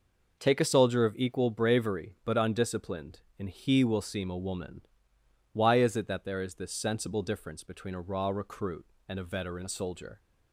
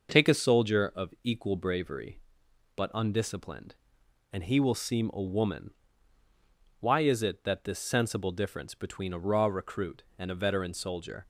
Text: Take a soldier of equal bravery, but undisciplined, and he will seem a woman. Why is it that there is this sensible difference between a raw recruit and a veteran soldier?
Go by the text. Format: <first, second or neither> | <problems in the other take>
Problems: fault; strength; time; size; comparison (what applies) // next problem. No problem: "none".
first | skips "there is"; at 7.6 s